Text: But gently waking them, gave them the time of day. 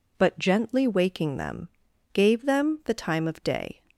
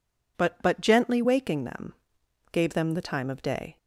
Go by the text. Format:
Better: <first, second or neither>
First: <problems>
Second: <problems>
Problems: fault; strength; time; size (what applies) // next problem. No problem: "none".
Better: first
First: none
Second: says "But" twice; at 0.6 s